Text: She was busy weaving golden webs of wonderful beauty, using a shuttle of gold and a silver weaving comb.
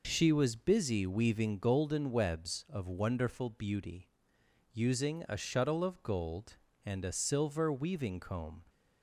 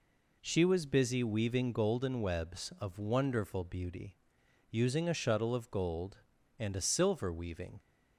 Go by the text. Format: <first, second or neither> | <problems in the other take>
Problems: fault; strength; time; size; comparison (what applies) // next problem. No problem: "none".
first | stops before "comb"; at 7.7 s